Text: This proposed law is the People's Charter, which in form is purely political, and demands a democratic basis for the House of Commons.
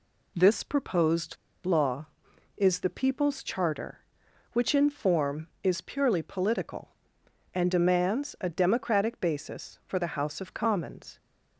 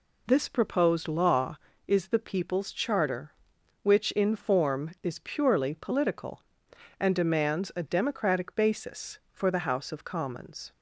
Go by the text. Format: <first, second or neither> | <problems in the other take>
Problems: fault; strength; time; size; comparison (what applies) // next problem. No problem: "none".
second | pauses between "proposed" and "law"; slight; at 1.3 s; 0.29 s long